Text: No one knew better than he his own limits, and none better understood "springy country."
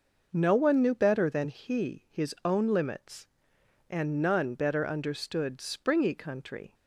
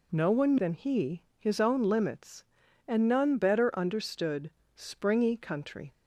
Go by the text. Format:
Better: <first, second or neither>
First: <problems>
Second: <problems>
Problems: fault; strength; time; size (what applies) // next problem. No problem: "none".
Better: first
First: none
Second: skips "knew better"; at 0.5 s // pauses between "he" and "his"; slight; at 1.2 s; 0.16 s long // pauses between "understood" and "springy"; slight; at 4.5 s; 0.24 s long